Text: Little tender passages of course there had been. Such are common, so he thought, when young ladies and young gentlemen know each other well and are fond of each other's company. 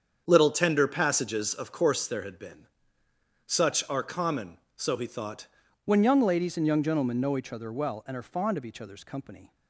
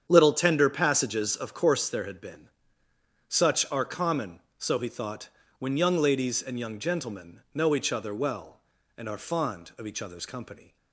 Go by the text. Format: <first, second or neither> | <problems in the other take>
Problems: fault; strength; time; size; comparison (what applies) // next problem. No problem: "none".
second | starts louder than the rest; strong; until 1.2 s; 7.5 dB; strong in the second // changes voice at "when"; from 5.8 s on; 3.7 s long